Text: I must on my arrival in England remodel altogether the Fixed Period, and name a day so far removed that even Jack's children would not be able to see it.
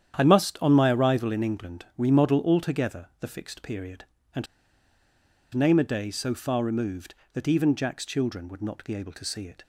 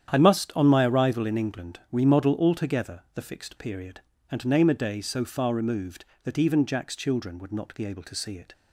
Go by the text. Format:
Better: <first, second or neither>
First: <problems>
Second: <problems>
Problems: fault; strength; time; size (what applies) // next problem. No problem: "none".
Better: second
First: starts louder than the rest; strong; until 1.2 s; 9.5 dB // pauses between "and" and "name"; at 4.4 s; 1.0 s long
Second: starts louder than the rest; strong; until 1.1 s; 9.5 dB